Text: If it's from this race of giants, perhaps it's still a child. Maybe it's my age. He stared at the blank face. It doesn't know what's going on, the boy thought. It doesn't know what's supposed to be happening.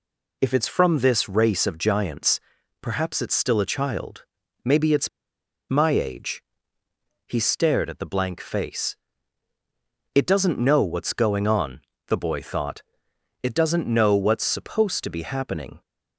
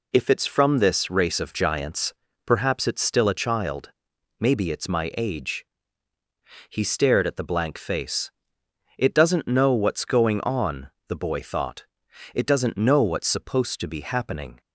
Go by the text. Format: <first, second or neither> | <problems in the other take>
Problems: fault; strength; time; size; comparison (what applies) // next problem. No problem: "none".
second | pauses between "it's" and "my"; noticeable; at 5.0 s; 0.60 s long